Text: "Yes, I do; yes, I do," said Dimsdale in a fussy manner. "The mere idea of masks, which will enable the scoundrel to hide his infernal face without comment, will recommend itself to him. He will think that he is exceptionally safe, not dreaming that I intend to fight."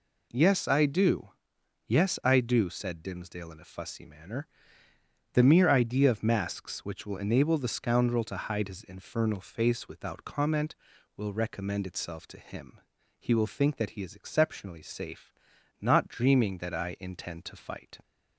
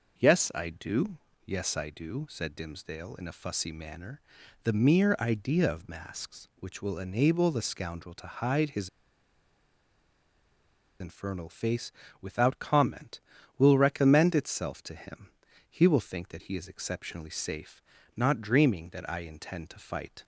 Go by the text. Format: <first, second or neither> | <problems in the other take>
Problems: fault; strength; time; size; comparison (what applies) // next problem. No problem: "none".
first | pauses between "his" and "infernal"; strong; at 8.8 s; 2.1 s long // pauses between "face" and "without"; slight; at 11.9 s; 0.28 s long